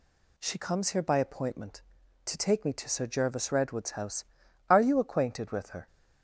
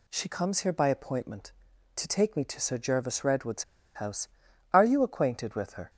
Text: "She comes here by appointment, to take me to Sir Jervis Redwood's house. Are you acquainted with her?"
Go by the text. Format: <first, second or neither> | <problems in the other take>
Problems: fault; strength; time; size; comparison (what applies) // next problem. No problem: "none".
first | pauses between "Redwood's" and "house"; slight; at 3.6 s; 0.31 s long